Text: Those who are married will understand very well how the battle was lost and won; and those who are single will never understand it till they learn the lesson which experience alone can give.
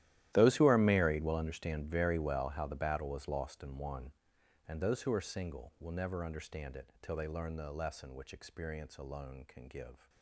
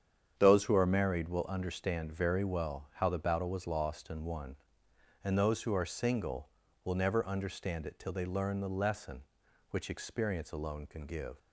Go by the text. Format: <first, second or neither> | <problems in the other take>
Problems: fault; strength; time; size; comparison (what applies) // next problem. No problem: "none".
second | gets quieter; strong; throughout; 18.5 dB // starts louder than the rest; strong; until 1.3 s; 13.5 dB; strong in the second